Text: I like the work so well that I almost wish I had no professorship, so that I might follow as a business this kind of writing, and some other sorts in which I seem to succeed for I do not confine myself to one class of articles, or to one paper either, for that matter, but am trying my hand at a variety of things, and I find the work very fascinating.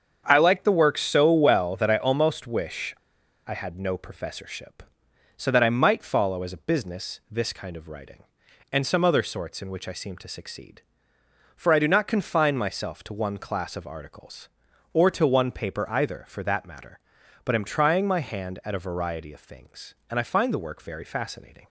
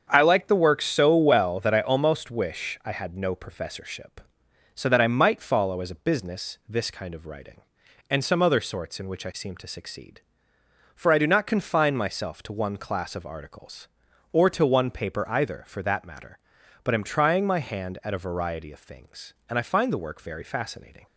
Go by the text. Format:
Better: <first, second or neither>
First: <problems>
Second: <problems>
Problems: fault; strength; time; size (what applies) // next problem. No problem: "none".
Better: second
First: starts louder than the rest; strong; until 1.2 s; 7.5 dB // pauses between "wish" and "I"; noticeable; at 2.9 s; 0.49 s long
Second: starts louder than the rest; strong; until 1.1 s; 7.5 dB